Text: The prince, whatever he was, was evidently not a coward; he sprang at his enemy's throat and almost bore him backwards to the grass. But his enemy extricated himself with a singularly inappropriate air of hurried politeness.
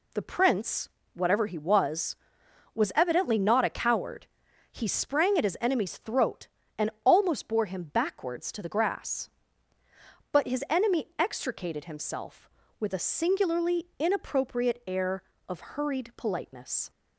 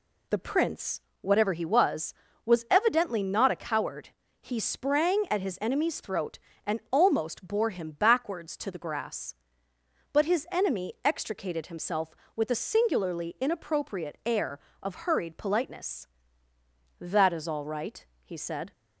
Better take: first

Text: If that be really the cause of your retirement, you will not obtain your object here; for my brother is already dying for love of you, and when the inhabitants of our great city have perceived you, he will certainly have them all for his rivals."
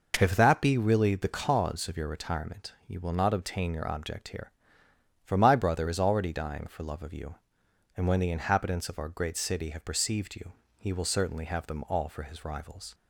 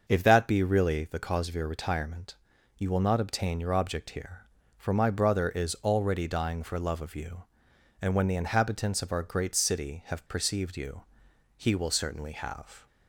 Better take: first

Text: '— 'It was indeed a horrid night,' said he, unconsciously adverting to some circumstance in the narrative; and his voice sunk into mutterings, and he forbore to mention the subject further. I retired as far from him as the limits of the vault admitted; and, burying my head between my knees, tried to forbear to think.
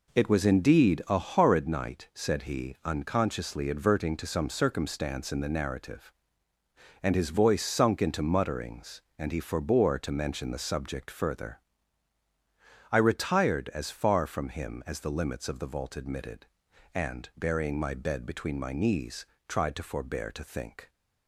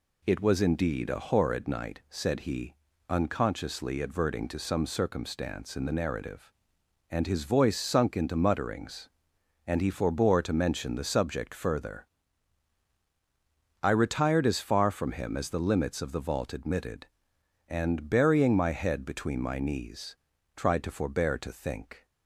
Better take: second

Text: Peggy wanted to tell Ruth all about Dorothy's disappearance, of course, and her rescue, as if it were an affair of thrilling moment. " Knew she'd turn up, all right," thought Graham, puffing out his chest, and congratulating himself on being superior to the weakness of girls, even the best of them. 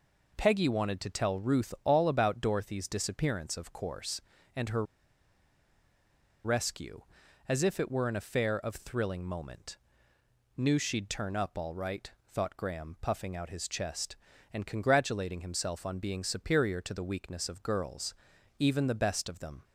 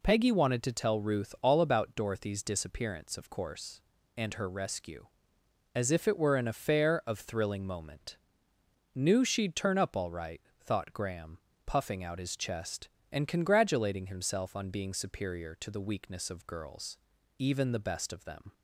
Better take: second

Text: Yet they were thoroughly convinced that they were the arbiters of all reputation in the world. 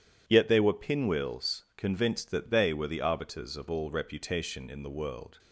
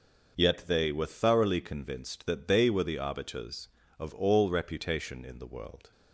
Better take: second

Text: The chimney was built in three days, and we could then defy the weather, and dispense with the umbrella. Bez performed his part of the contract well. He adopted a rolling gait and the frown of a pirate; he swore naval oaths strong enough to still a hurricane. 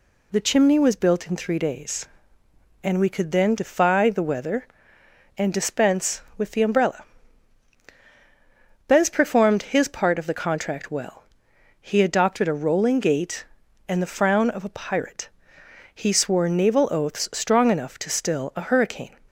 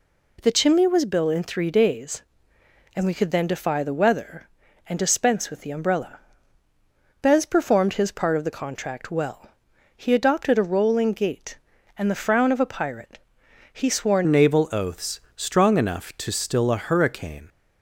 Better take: first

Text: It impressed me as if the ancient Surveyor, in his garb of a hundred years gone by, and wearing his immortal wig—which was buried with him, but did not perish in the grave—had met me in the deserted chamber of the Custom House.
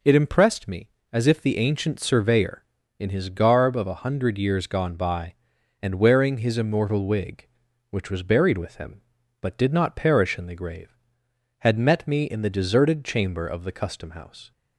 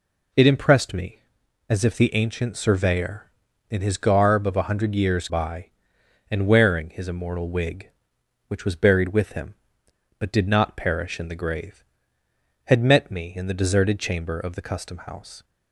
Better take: first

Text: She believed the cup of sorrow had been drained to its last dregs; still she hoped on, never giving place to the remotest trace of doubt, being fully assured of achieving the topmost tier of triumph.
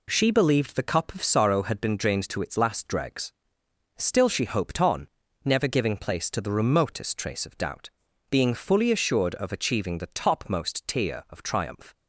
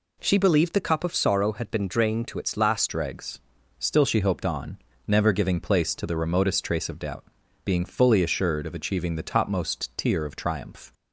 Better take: first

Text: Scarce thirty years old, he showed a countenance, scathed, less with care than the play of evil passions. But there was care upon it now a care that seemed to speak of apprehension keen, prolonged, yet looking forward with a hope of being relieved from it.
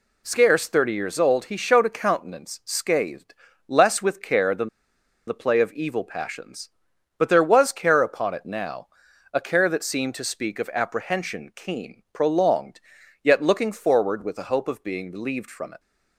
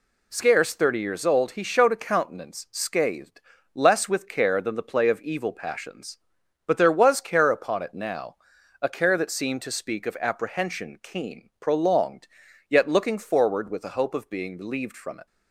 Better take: second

